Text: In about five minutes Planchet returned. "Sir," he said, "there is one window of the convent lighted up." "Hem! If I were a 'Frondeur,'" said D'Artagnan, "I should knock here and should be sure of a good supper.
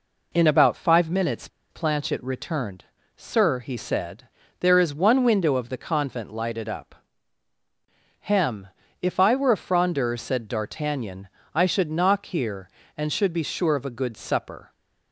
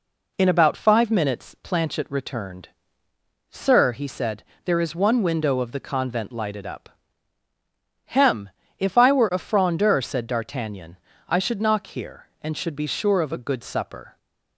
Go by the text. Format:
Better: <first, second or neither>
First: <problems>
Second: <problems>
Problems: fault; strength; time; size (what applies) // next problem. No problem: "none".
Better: second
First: pauses between "minutes" and "Planchet"; slight; at 1.4 s; 0.22 s long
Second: none